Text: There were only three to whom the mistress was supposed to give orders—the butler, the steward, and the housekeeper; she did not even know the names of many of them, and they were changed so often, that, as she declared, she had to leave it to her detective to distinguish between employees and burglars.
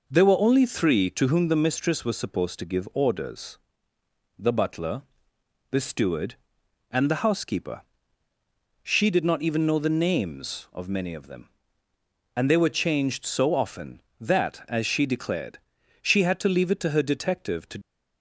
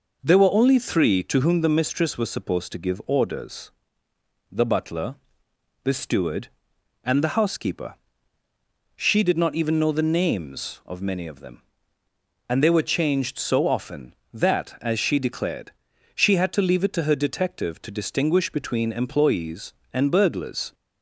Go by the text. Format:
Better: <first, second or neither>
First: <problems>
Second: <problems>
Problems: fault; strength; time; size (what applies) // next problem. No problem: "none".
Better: second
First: stops before "distinguish between employees and burglars"; at 17.8 s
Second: none